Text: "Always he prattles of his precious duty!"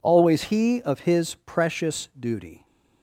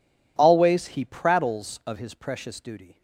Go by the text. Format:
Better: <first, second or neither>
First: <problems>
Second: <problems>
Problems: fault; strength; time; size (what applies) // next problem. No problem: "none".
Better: second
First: skips "prattles"; at 0.8 s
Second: none